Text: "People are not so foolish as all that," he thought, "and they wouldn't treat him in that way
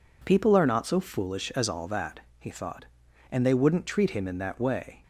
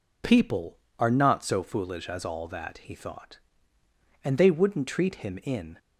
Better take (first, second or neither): first